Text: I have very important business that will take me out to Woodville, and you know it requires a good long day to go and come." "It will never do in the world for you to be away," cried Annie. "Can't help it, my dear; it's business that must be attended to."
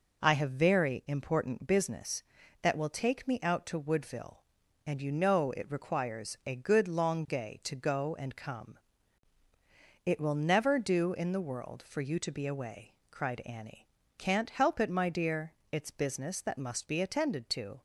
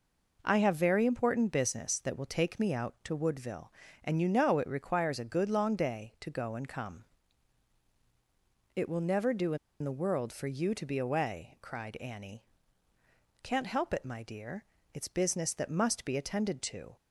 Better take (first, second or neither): first